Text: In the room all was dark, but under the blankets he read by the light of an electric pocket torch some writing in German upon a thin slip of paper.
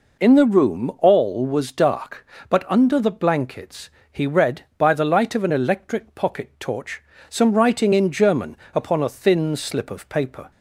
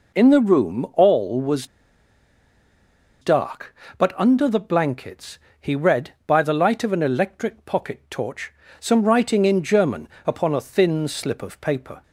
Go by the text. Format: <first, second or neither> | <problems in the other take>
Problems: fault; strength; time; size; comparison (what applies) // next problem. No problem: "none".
first | pauses between "was" and "dark"; strong; at 1.6 s; 1.5 s long // pauses between "blankets" and "he"; slight; at 5.3 s; 0.22 s long; slight in the first // pauses between "torch" and "some"; slight; at 8.5 s; 0.26 s long; slight in the first // pauses between "German" and "upon"; slight; at 10.0 s; 0.20 s long; slight in the first